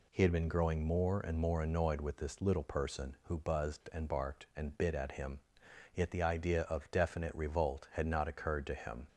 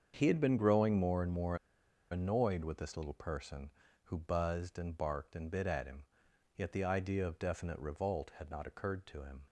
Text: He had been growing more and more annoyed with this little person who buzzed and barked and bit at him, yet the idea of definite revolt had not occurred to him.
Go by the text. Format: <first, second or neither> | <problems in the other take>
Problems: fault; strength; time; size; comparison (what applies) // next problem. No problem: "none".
first | starts louder than the rest; strong; until 1.1 s; 7 dB // pauses between "more" and "annoyed"; noticeable; at 1.5 s; 0.54 s long